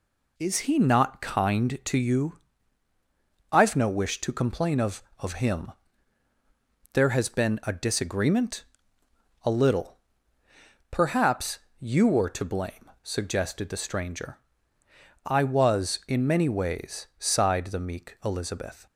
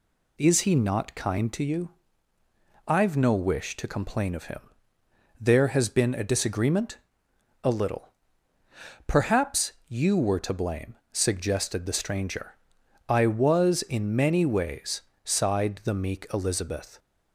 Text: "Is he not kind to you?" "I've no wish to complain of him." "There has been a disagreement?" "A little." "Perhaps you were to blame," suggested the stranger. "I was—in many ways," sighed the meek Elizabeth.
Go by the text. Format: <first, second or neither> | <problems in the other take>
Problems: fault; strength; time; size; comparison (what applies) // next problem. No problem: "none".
second | says "of" twice; at 5.1 s // pauses between "Perhaps" and "you"; slight; at 11.5 s; 0.20 s long; slight in the second